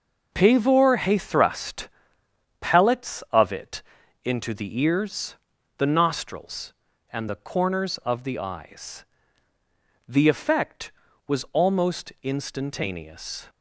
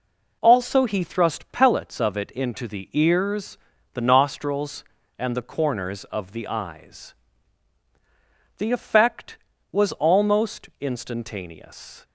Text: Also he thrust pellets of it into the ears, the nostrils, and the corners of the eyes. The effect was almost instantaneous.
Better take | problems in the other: second | says "Pavor" for "Also"; at 0.3 s // pauses between "thrust" and "pellets"; noticeable; at 1.8 s; 0.72 s long // pauses between "it" and "into"; at 3.8 s; 0.42 s long

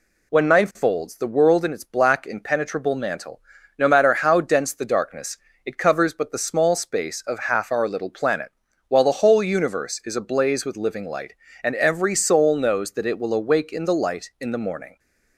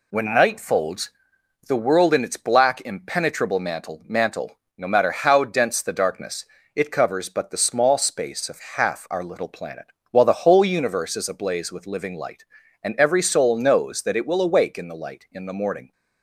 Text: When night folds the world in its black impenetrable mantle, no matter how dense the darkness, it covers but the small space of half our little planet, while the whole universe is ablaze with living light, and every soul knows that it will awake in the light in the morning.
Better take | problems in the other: first | pauses between "folds" and "the"; noticeable; at 1.1 s; 0.56 s long // says "mantle" twice; at 4.0 s // pauses between "of" and "half"; slight; at 8.5 s; 0.16 s long

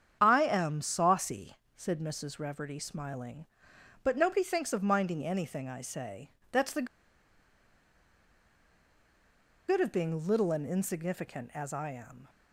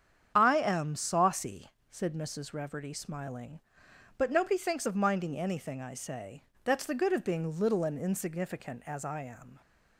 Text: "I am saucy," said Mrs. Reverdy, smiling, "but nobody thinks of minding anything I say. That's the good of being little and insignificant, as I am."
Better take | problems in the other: second | starts louder than the rest; strong; until 1.2 s; 8 dB; strong in the second // pauses between "the" and "good"; strong; at 6.8 s; 2.8 s long

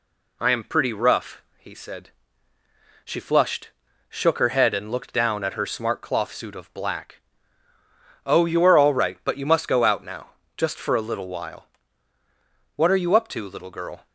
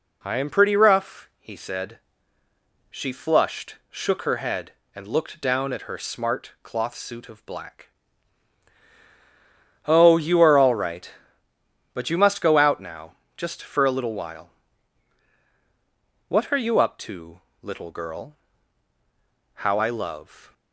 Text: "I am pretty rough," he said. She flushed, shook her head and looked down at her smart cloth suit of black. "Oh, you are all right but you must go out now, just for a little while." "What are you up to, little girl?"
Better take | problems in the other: first | goes on to say "How I love"; noticeable; from 19.5 s on; 0.98 s long

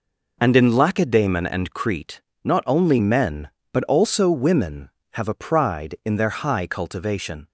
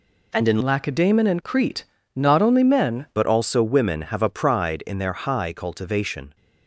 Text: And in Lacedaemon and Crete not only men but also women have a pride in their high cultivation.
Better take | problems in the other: first | changes voice from "Lacedaemon" to "men"; from 0.6 to 3.0 s; 2.4 s long // pauses between "Crete" and "not"; slight; at 1.8 s; 0.32 s long; slight in the first

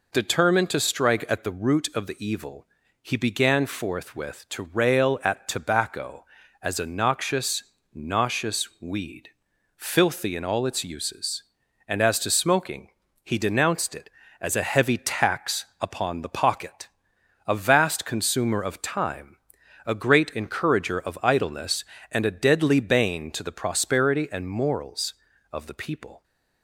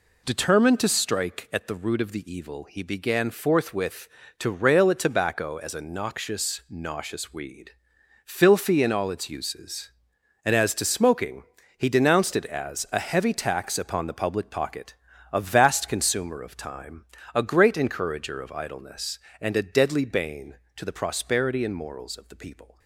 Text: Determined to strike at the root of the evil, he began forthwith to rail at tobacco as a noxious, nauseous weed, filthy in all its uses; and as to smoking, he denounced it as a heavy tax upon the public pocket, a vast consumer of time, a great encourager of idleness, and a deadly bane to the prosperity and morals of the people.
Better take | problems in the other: second | skips "public"; at 16.2 s

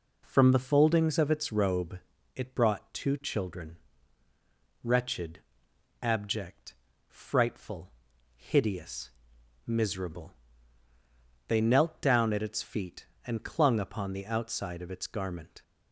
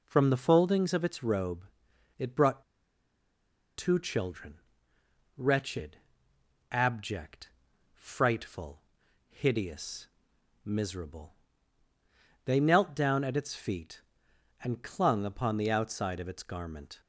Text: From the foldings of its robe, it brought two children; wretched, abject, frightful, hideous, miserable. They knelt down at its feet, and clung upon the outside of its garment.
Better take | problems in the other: first | pauses between "brought" and "two"; at 2.6 s; 1.1 s long

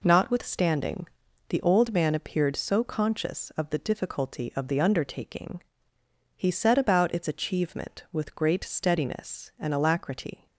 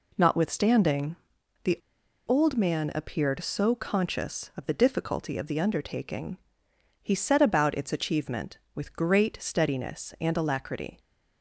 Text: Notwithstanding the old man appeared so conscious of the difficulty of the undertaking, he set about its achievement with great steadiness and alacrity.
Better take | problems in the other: first | pauses between "Notwithstanding" and "the"; noticeable; at 1.1 s; 0.48 s long; also in the first // pauses between "the" and "old"; noticeable; at 1.7 s; 0.47 s long

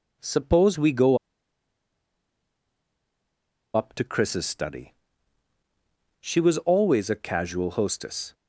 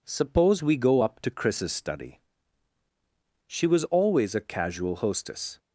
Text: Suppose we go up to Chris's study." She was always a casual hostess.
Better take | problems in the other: second | pauses between "go" and "up"; strong; at 1.1 s; 2.5 s long

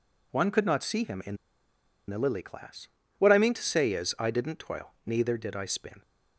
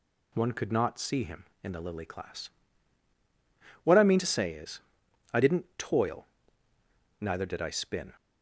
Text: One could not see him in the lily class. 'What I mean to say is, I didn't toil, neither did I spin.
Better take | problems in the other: second | pauses between "in" and "the"; noticeable; at 1.3 s; 0.72 s long

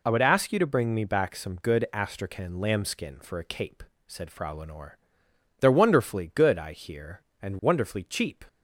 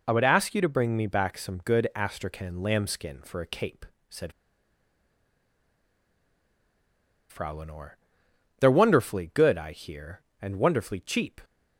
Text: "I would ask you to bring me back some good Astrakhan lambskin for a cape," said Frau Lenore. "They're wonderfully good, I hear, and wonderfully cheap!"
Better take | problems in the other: first | pauses between "said" and "Frau"; strong; at 4.3 s; 2.9 s long

